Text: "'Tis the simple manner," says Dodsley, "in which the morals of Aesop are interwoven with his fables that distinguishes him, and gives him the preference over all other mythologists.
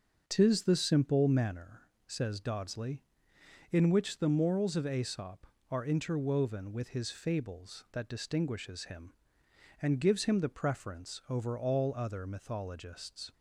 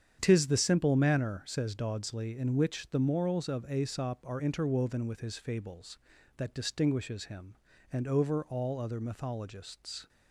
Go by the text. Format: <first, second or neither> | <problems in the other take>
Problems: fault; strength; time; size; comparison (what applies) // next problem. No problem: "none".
first | starts louder than the rest; strong; until 1.2 s; 8.5 dB; noticeable in the first // skips "gives him the preference"; at 8.0 s